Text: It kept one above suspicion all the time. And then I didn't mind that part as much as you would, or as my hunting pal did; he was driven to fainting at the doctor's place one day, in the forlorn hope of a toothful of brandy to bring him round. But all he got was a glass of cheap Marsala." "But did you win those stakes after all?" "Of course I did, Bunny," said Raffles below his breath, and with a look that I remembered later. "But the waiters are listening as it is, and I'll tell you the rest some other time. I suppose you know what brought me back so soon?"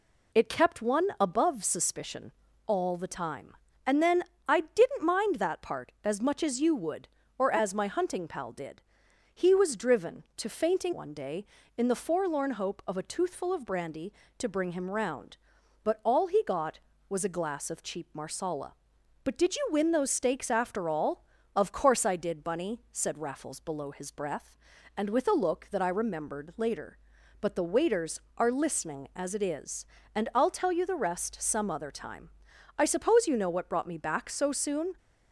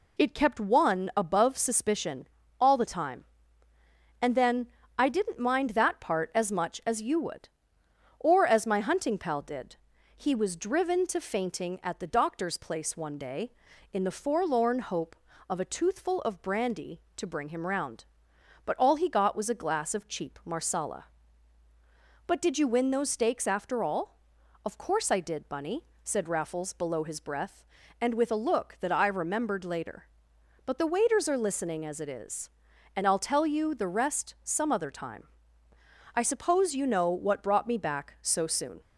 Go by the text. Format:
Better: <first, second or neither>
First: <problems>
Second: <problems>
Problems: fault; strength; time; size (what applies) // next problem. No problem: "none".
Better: second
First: pauses between "suspicion" and "all"; slight; at 2.3 s; 0.34 s long // pauses between "then" and "I"; slight; at 4.2 s; 0.26 s long // skips "at the doctor's place"; at 10.9 s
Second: pauses between "suspicion" and "all"; slight; at 2.2 s; 0.34 s long // pauses between "then" and "I"; slight; at 4.6 s; 0.32 s long